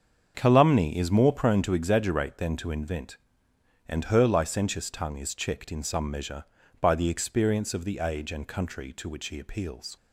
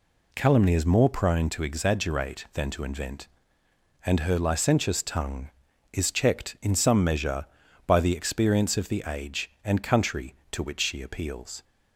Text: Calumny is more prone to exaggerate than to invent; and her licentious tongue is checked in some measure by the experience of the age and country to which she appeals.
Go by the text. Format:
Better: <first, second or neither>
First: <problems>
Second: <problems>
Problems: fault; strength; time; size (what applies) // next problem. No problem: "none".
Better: second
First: starts louder than the rest; until 1.3 s; 7 dB // says "he" for "she"; at 9.2 s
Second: none